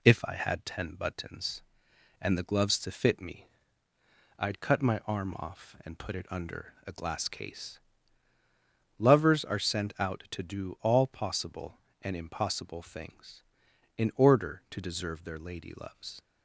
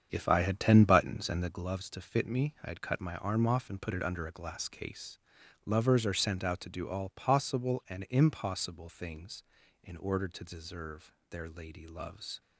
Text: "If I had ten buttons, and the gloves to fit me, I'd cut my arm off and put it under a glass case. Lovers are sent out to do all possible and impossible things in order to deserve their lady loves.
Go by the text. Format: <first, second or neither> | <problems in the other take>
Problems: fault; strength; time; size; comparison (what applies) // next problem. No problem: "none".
first | starts louder than the rest; strong; until 1.6 s; 7.5 dB // pauses between "deserve" and "their"; slight; at 11.1 s; 0.18 s long